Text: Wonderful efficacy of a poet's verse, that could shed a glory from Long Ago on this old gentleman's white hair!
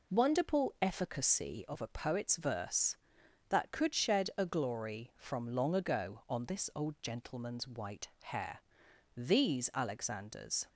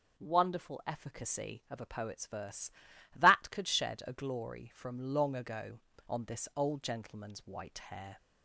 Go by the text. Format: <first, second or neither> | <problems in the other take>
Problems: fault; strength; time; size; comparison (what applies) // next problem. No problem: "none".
second | goes on to say "These Alexanders"; from 9.1 s on; 1.5 s long